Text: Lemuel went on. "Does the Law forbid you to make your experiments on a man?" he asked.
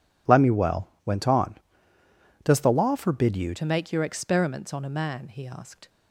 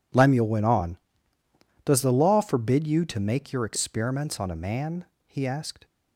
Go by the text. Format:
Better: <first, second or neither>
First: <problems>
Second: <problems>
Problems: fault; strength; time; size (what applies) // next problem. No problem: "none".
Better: second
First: pauses between "Lemuel" and "went"; slight; at 0.8 s; 0.18 s long // changes voice at "to"; from 3.5 s on; 2.3 s long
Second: none